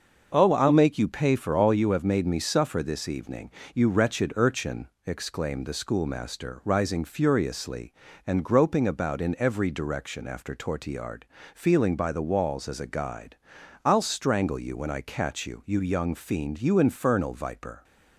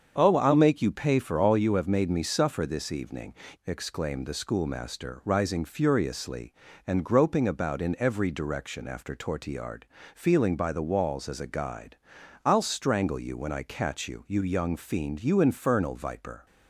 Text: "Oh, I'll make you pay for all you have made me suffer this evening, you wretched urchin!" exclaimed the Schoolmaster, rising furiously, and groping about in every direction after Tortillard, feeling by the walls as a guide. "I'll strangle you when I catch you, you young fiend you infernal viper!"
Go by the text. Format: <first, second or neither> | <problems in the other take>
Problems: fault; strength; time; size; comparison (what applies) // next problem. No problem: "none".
first | starts louder than the rest; strong; until 1.1 s; 7.5 dB; also in the first // skips "you wretched urchin"; at 3.4 s